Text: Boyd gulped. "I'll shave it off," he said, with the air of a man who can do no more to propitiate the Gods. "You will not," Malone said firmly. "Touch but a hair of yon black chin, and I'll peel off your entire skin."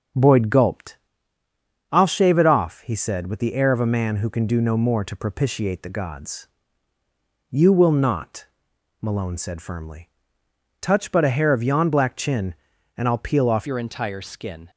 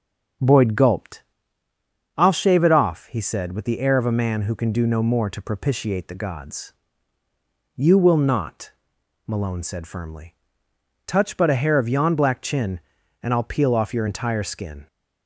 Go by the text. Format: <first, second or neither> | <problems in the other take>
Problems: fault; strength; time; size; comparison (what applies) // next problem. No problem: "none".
second | starts louder than the rest; strong; until 2.0 s; 7 dB; strong in the second // changes voice at "your"; from 13.6 s on; 1.0 s long